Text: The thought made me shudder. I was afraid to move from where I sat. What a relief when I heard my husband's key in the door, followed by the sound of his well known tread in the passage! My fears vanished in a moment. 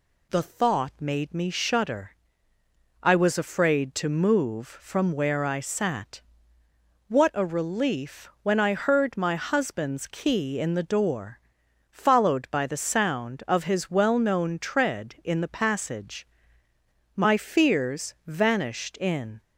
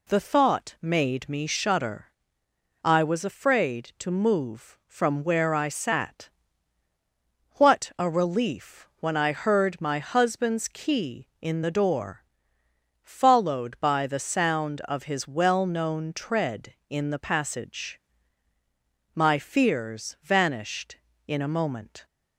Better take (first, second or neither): second